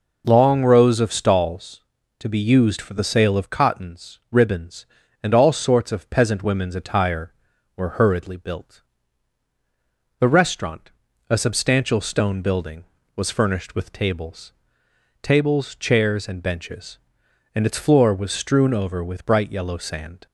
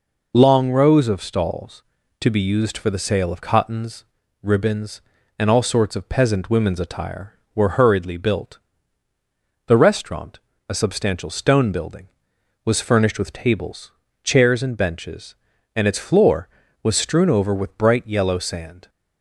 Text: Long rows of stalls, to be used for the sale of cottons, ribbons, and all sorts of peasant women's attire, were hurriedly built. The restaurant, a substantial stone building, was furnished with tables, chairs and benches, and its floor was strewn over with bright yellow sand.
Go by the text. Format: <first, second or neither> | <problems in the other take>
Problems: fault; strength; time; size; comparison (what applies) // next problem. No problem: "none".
second | says "tables" twice; at 15.2 s